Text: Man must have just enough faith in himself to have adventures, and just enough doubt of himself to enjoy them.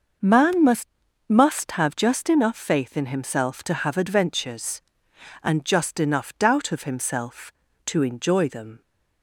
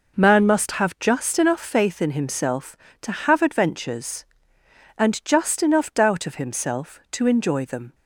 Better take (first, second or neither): second